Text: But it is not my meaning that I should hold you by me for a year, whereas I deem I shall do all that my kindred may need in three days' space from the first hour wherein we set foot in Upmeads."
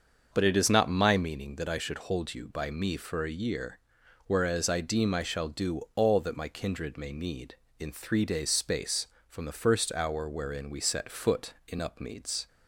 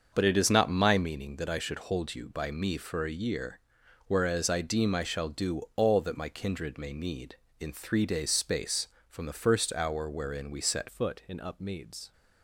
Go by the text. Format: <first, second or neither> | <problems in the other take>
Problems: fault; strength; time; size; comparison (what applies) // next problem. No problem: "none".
first | starts louder than the rest; until 1.1 s; 6.5 dB; also in the first // changes voice at "foot"; from 10.8 s on; 1.3 s long